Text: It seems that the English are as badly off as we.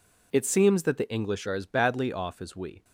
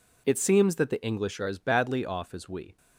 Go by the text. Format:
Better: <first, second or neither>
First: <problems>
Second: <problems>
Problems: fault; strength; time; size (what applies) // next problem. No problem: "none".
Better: neither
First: none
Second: none